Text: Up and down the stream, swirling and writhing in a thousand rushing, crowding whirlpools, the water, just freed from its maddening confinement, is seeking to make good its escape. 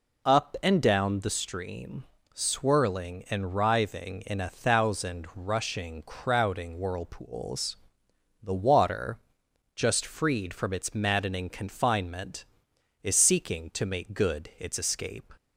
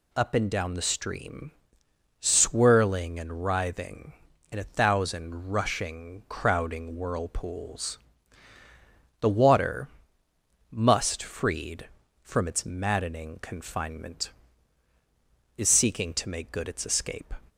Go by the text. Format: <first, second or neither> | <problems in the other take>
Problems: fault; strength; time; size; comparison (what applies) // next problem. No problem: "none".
first | says "must" for "just"; at 10.6 s